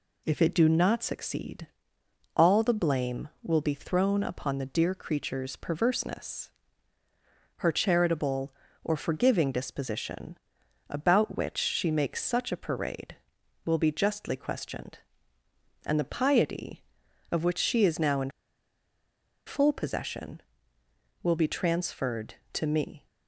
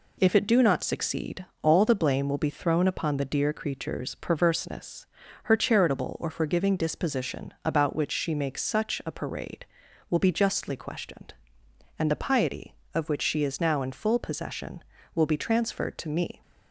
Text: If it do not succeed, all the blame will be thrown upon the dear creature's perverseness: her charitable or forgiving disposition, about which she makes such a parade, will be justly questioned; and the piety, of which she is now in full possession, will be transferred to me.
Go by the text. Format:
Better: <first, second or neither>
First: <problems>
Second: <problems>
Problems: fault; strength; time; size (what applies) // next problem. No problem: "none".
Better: second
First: pauses between "in" and "full"; at 18.2 s; 1.1 s long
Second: none